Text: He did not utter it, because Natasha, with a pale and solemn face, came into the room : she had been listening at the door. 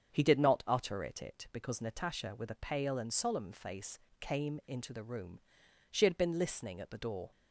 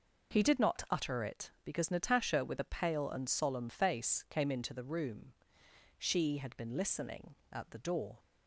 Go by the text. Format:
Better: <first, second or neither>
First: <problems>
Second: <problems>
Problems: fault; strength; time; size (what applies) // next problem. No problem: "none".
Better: second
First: starts louder than the rest; strong; until 1.1 s; 7.5 dB // says "it" twice; at 1.2 s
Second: none